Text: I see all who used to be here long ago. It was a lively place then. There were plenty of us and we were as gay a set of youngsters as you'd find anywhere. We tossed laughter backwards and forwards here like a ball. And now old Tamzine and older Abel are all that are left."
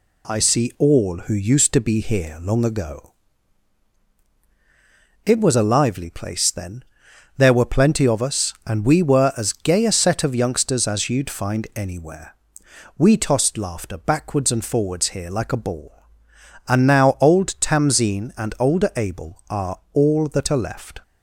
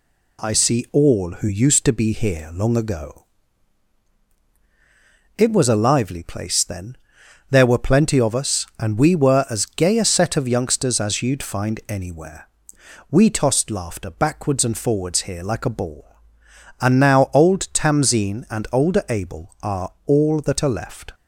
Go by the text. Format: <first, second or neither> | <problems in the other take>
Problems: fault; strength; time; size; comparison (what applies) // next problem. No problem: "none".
neither | none